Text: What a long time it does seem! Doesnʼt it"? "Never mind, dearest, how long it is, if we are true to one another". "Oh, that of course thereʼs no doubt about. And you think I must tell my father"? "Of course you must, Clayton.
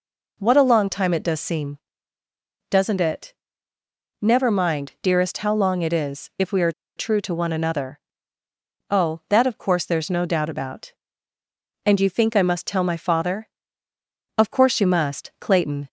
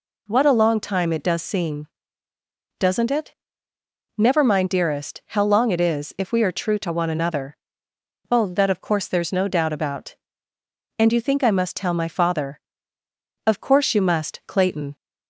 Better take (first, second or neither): second